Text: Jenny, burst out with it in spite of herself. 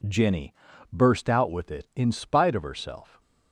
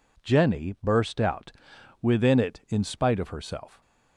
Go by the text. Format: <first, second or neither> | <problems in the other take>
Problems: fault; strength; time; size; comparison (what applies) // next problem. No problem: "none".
first | says "within" for "with"; at 2.0 s